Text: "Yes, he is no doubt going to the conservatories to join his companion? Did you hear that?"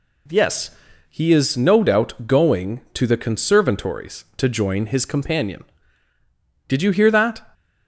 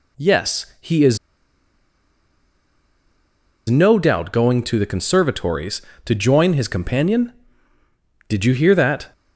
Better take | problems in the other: first | pauses between "is" and "no"; strong; at 1.1 s; 2.5 s long

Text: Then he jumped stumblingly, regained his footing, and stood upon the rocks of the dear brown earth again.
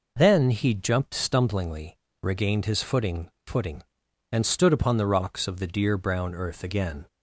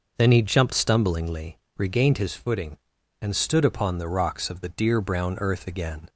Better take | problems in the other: second | says "footing" twice; at 3.4 s

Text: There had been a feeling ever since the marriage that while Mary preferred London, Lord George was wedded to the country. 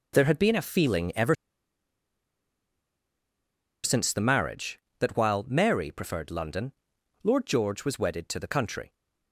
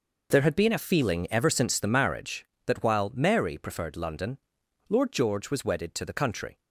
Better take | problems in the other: second | pauses between "ever" and "since"; strong; at 1.3 s; 2.4 s long

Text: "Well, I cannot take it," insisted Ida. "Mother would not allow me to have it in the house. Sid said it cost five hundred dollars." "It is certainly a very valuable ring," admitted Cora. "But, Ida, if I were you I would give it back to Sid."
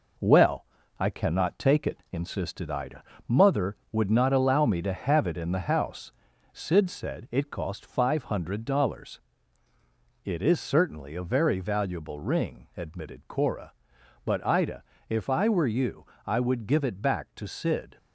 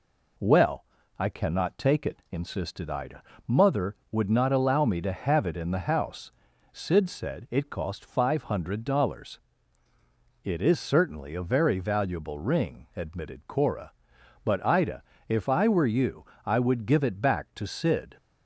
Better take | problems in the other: second | gets quieter; noticeable; throughout; 4 dB // pauses between "you" and "I"; slight; at 16.0 s; 0.18 s long; slight in the second

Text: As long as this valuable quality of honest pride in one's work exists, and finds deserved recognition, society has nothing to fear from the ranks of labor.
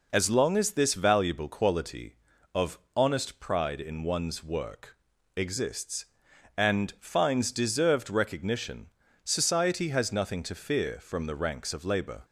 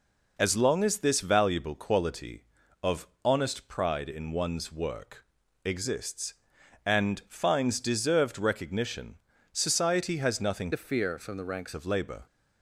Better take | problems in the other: first | pauses between "of" and "honest"; slight; at 3.0 s; 0.18 s long; slight in the first // pauses between "work" and "exists"; at 5.2 s; 0.40 s long; also in the first // changes voice from "to" to "ranks"; from 10.7 to 11.7 s; 1.0 s long

